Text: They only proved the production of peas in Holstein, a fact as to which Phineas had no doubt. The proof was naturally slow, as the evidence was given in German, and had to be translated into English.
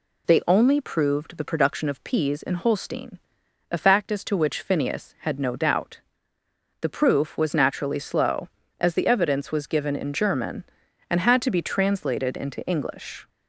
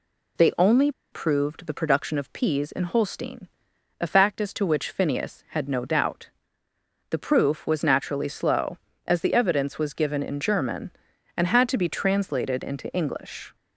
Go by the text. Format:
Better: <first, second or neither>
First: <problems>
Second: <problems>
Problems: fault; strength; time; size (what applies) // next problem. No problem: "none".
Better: first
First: none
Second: pauses between "only" and "proved"; slight; at 0.9 s; 0.21 s long